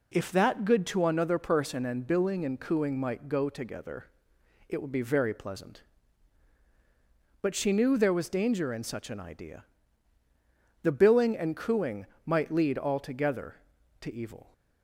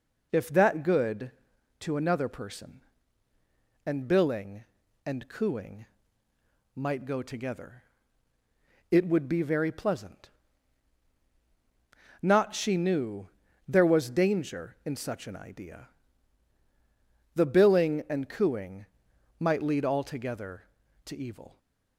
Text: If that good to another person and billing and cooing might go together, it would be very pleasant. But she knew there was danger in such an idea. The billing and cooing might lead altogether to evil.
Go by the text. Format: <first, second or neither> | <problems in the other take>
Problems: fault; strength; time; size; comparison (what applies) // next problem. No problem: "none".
first | pauses between "cooing" and "might"; noticeable; at 5.8 s; 0.90 s long // says "Not" for "But"; at 12.2 s // pauses between "knew" and "there"; at 13.2 s; 0.40 s long // pauses between "cooing" and "might"; noticeable; at 18.8 s; 0.56 s long; slight in the first